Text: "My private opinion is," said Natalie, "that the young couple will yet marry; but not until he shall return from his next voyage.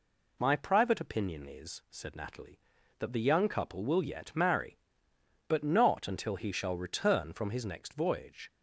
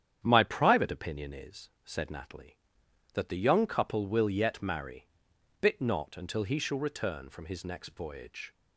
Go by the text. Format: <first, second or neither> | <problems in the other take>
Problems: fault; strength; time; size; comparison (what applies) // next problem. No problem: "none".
first | starts louder than the rest; strong; until 1.2 s; 9.5 dB // says "bit" for "but"; at 5.6 s